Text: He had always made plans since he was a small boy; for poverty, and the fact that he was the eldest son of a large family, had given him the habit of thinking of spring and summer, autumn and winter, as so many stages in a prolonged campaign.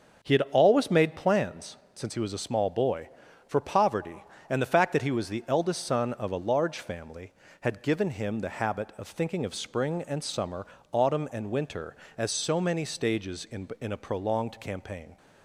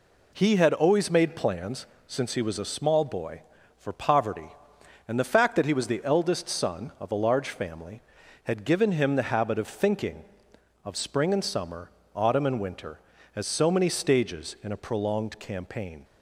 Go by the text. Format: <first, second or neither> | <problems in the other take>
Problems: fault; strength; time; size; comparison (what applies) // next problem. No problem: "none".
second | starts louder than the rest; until 1.3 s; 7 dB // pauses between "plans" and "since"; slight; at 1.7 s; 0.18 s long; slight in the second // says "in" twice; at 13.8 s